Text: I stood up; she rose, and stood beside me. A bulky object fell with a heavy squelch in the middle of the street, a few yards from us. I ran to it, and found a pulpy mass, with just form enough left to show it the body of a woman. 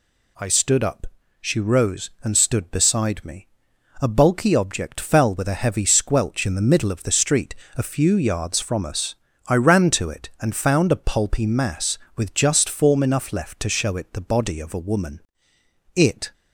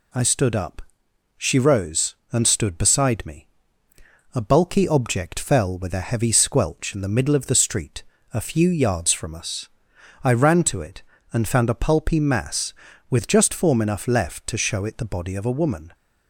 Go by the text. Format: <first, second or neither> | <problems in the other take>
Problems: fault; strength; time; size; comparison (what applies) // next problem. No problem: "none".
second | goes on to say "It"; slight; from 15.9 s on; 0.38 s long